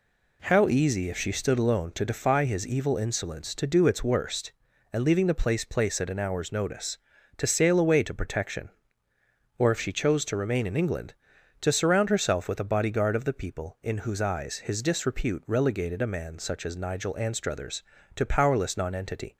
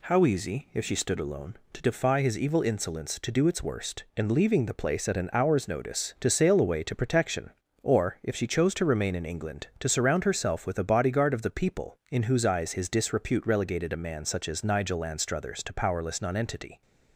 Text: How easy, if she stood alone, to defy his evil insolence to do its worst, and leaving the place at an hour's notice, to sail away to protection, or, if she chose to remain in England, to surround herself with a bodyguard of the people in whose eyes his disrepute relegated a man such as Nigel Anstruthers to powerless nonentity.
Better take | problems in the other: second | says "place" twice; at 5.6 s

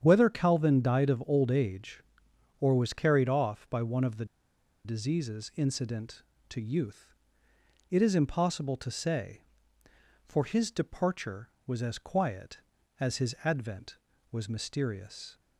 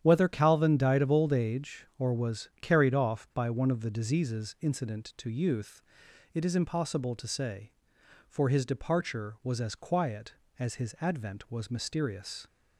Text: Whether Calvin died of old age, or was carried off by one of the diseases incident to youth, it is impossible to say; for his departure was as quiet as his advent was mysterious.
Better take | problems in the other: second | starts louder than the rest; strong; until 1.0 s; 8.5 dB; strong in the second // pauses between "the" and "diseases"; noticeable; at 4.2 s; 0.58 s long

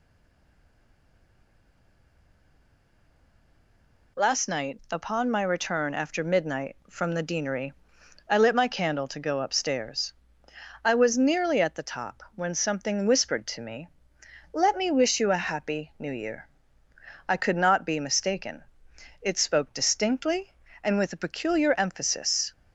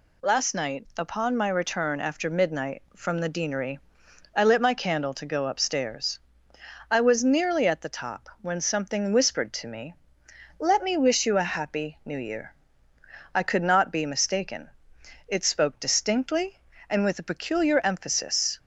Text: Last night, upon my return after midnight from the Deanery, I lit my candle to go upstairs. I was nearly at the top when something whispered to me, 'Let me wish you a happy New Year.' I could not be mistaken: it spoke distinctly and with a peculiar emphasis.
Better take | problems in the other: second | stays silent before the first word; strong; until 4.1 s; 4.1 s long

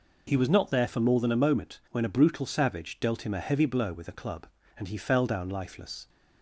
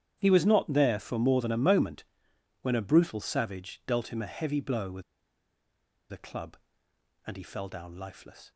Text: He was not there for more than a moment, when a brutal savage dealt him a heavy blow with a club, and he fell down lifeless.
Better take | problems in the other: first | starts louder than the rest; strong; until 1.2 s; 9.5 dB // pauses between "with" and "a"; at 5.0 s; 1.0 s long

